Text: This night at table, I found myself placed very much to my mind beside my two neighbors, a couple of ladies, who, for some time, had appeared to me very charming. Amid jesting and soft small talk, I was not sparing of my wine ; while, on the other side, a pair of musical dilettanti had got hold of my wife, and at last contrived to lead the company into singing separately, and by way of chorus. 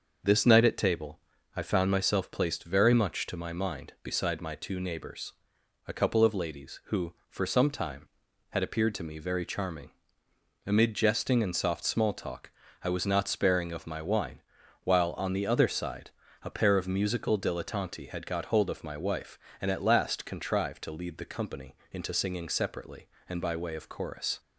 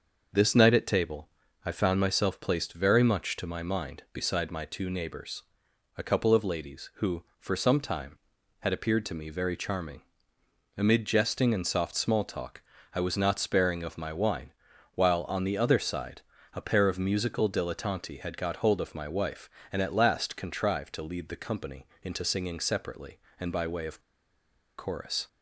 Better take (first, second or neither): first